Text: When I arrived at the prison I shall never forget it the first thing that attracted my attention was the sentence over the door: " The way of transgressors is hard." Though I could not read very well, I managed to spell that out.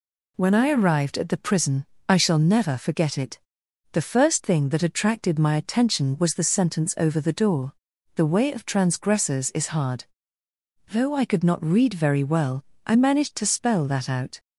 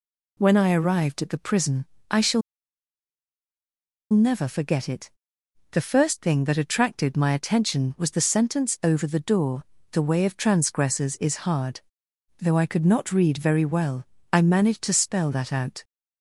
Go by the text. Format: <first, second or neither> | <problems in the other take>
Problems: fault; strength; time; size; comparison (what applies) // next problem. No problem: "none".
first | pauses between "prison" and "I"; slight; at 1.8 s; 0.28 s long; slight in the first // pauses between "shall" and "never"; strong; at 2.4 s; 1.7 s long // pauses between "it" and "the"; noticeable; at 5.0 s; 0.62 s long; noticeable in the first